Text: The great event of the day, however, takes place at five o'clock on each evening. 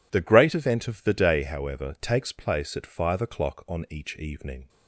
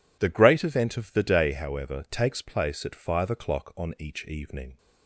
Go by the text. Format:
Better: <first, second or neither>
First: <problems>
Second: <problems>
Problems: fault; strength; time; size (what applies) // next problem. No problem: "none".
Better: neither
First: none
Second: none